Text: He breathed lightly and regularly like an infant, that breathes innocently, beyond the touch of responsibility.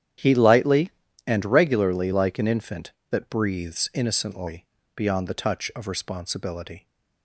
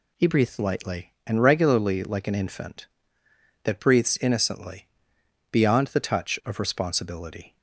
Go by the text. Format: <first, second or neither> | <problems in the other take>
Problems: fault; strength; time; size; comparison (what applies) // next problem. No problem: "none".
second | starts louder than the rest; strong; until 1.5 s; 9.5 dB // skips "breathed"; at 0.3 s